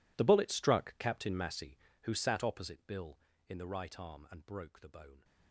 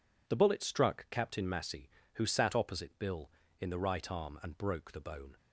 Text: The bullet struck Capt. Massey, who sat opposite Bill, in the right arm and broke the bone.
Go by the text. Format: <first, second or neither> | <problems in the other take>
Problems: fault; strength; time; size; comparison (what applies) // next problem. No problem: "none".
second | gets quieter; strong; throughout; 21.5 dB